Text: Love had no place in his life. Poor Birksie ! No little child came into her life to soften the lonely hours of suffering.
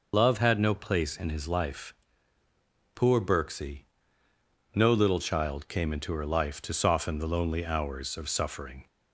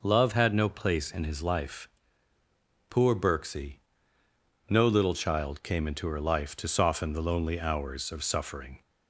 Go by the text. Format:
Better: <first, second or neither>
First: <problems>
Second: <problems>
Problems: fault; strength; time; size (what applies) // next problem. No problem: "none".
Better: second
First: loses the start of "Love"; at 0.1 s; 55 ms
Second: none